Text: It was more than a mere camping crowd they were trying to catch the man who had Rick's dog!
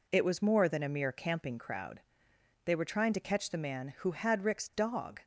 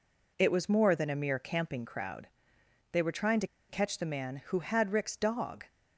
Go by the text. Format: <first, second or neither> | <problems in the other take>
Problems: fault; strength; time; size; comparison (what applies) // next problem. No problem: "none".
first | pauses between "crowd" and "they"; noticeable; at 2.2 s; 0.64 s long; noticeable in the first // pauses between "to" and "catch"; slight; at 3.4 s; 0.22 s long